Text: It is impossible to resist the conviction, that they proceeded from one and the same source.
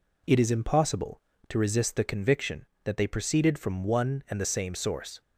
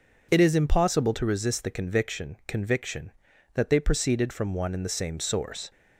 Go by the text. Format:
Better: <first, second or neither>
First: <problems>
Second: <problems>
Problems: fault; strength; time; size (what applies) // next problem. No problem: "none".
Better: first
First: none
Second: says "conviction" twice; at 2.4 s